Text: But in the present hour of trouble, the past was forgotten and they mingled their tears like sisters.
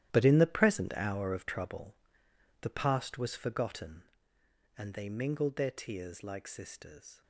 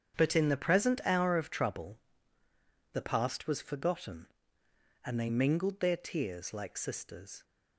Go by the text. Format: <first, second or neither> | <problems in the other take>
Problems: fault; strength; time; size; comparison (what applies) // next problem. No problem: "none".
second | gets quieter; strong; throughout; 13.5 dB // starts louder than the rest; strong; until 1.1 s; 12 dB; strong in the second